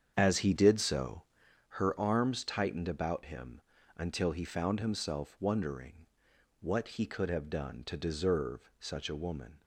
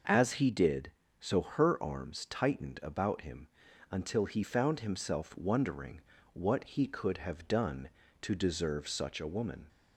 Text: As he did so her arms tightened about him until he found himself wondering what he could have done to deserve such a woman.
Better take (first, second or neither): second